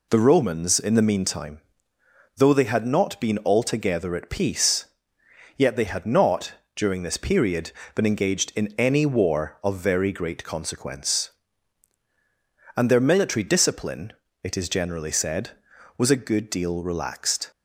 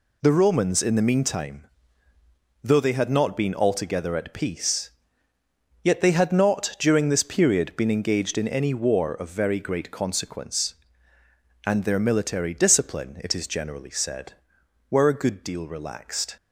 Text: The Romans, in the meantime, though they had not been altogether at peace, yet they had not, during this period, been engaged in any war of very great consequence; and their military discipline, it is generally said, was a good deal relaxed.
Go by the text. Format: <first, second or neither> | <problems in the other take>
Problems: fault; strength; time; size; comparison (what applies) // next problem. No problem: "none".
first | says "were" for "was"; at 14.9 s